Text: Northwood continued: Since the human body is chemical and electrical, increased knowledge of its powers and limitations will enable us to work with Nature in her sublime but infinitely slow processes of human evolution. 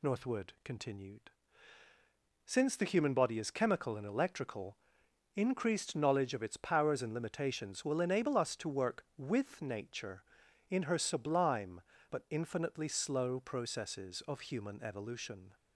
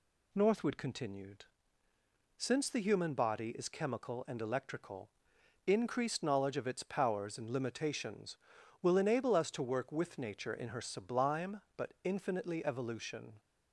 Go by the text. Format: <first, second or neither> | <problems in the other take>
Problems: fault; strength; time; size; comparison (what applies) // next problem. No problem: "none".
first | skips "slow processes of human"; at 12.6 s